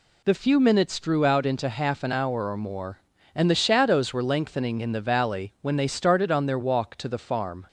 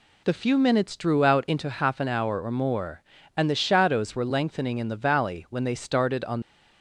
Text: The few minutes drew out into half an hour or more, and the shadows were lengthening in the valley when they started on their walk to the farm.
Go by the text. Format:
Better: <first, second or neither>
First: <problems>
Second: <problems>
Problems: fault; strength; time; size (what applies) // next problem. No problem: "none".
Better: first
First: none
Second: stops before "their walk to the farm"; at 6.4 s